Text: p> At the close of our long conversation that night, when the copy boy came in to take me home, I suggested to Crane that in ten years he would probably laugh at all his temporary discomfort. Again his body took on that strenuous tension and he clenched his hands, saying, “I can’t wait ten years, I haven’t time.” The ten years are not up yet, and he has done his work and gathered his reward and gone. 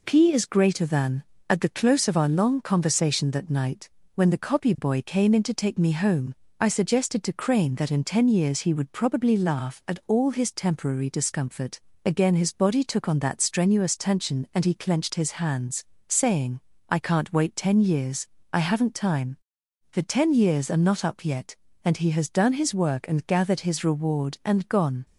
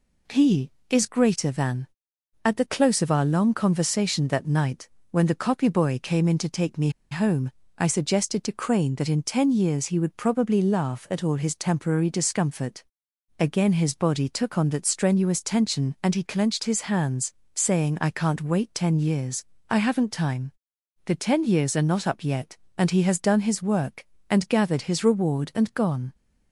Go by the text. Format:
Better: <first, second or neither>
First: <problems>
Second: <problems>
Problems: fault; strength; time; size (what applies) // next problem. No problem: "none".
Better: first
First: none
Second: pauses between "me" and "home"; slight; at 6.8 s; 0.21 s long